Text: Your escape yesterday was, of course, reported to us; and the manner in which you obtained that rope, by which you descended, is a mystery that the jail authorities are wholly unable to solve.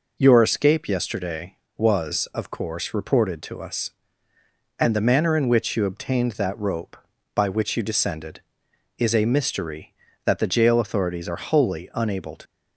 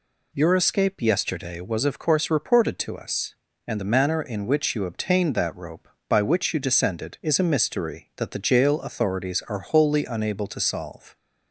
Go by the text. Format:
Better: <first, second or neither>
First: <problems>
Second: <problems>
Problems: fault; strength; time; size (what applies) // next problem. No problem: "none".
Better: second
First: stops before "solve"; at 12.4 s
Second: none